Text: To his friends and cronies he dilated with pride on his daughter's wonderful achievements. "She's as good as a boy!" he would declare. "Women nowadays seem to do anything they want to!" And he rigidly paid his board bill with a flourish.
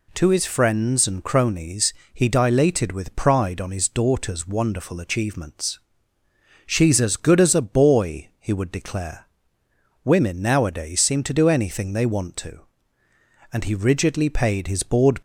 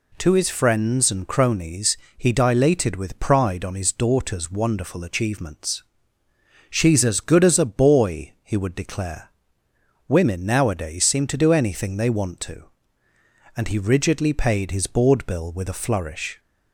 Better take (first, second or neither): second